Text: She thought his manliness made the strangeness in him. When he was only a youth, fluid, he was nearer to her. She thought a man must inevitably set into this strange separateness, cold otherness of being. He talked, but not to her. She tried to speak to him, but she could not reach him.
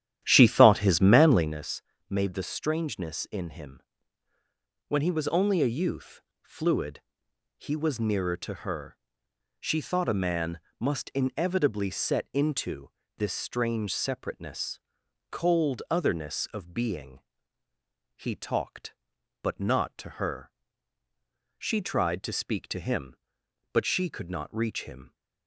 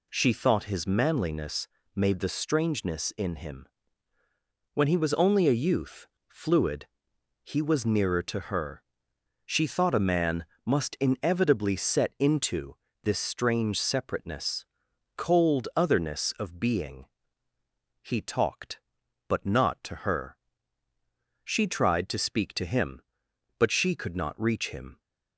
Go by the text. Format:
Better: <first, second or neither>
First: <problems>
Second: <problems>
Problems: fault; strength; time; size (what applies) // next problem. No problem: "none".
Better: second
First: starts louder than the rest; strong; until 1.6 s; 11.5 dB // pauses between "manliness" and "made"; slight; at 1.8 s; 0.28 s long // pauses between "man" and "must"; slight; at 10.5 s; 0.20 s long // pauses between "into" and "this"; slight; at 12.8 s; 0.28 s long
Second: pauses between "manliness" and "made"; slight; at 1.6 s; 0.28 s long // pauses between "man" and "must"; slight; at 10.4 s; 0.20 s long // pauses between "into" and "this"; slight; at 12.7 s; 0.28 s long